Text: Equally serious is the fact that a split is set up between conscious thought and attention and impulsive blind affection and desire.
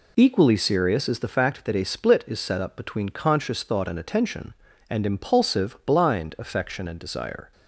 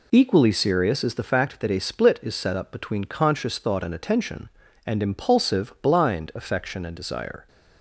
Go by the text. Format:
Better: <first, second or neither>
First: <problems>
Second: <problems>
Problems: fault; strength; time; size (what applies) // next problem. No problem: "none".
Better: neither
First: none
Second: none